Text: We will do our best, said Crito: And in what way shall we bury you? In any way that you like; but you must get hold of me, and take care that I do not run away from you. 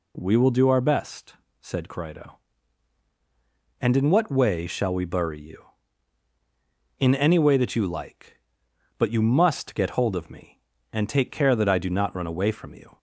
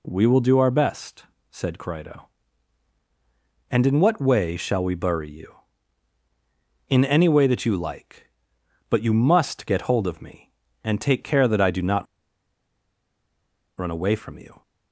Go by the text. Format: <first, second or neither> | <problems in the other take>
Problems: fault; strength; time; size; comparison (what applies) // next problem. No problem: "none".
first | pauses between "not" and "run"; strong; at 12.0 s; 1.7 s long